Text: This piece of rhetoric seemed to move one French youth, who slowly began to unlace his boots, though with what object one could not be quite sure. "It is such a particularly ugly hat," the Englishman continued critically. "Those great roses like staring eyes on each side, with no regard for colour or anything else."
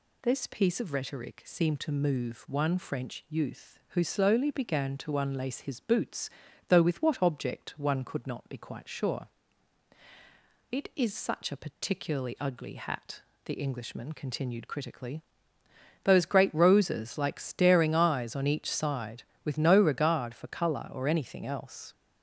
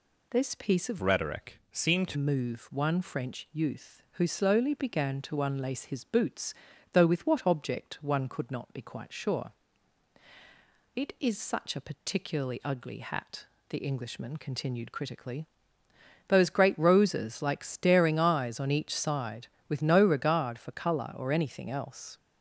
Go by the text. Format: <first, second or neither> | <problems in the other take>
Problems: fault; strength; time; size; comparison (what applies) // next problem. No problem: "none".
first | changes voice from "rhetoric" to "to"; from 1.0 to 2.1 s; 1.1 s long